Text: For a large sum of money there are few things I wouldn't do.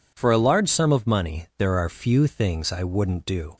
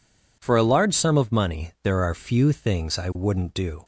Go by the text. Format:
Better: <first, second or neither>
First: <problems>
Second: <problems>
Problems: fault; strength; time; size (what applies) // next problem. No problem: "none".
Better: neither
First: none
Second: none